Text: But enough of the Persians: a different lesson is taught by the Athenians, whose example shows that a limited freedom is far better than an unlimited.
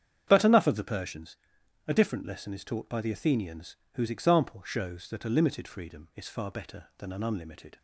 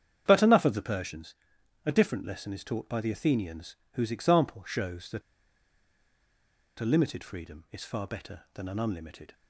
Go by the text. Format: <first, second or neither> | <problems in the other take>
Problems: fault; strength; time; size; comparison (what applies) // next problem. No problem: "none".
first | starts louder than the rest; strong; until 1.2 s; 8.5 dB; strong in the first // pauses between "that" and "a"; strong; at 5.2 s; 1.5 s long